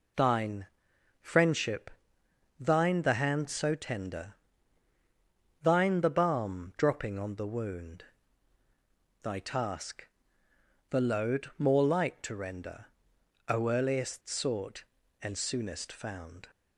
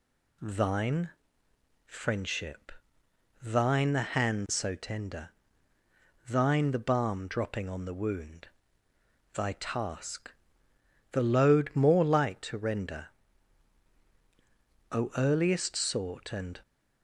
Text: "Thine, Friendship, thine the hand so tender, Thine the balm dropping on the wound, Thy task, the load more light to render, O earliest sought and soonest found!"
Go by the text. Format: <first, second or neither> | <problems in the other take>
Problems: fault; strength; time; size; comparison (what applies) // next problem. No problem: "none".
first | stops before "soonest found"; at 16.6 s